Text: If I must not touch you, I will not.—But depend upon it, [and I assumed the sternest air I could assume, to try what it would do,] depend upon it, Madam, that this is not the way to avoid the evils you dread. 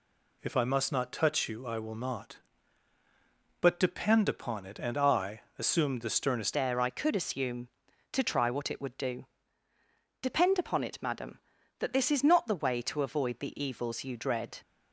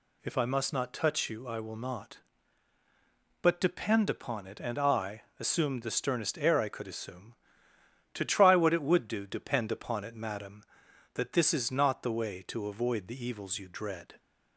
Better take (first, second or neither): second